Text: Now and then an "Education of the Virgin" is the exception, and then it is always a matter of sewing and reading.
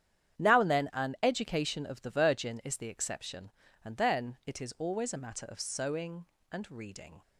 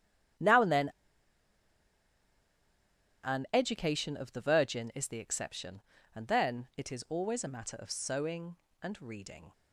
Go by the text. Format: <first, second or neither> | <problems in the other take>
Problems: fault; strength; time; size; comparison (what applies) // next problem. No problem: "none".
first | starts louder than the rest; strong; until 3.8 s; 9.5 dB; strong in the first // pauses between "then" and "an"; strong; at 0.8 s; 2.3 s long